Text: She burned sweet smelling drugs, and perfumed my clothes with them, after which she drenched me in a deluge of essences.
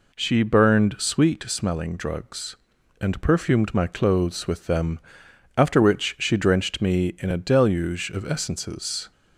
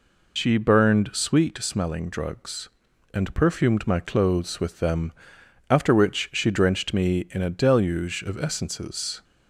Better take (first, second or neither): first